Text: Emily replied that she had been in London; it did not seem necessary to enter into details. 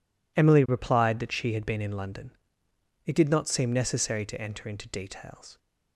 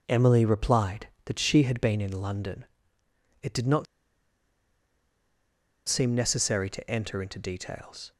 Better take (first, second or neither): first